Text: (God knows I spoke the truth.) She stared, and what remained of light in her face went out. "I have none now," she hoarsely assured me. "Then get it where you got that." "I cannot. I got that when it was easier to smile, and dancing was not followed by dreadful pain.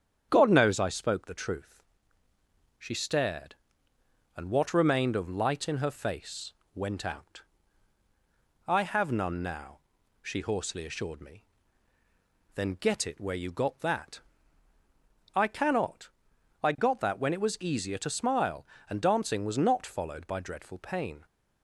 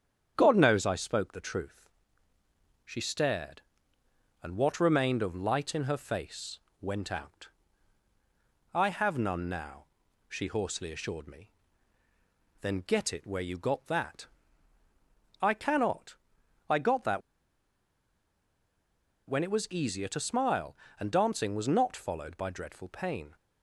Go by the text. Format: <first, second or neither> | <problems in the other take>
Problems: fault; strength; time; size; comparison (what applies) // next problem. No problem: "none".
first | starts louder than the rest; strong; until 1.3 s; 8.5 dB; strong in the first // pauses between "face" and "went"; slight; at 6.5 s; 0.22 s long; slight in the first // pauses between "that" and "when"; strong; at 17.2 s; 2.0 s long